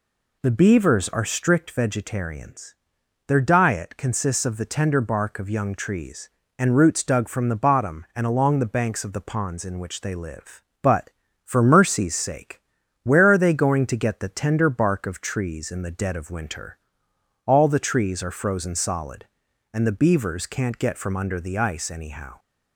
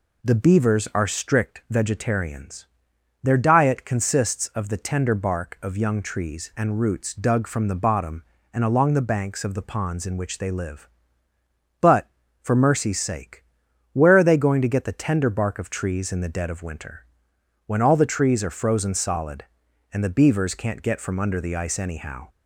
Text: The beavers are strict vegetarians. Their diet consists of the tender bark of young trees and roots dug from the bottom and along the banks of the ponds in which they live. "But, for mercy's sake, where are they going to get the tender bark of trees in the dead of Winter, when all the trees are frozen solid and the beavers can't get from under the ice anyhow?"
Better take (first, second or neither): second